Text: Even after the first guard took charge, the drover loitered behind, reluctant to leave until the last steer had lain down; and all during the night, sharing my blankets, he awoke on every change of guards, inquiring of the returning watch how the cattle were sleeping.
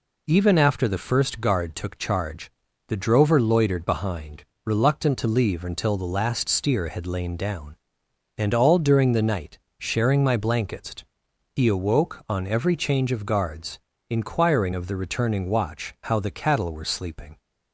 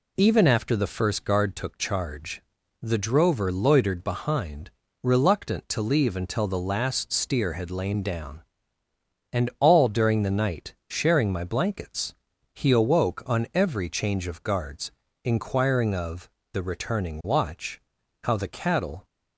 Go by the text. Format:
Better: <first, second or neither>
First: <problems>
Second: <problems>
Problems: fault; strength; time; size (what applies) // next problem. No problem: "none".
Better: first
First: none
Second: pauses between "of" and "the"; slight; at 16.2 s; 0.24 s long // pauses between "watch" and "how"; at 17.8 s; 0.44 s long // stops before "were sleeping"; at 19.0 s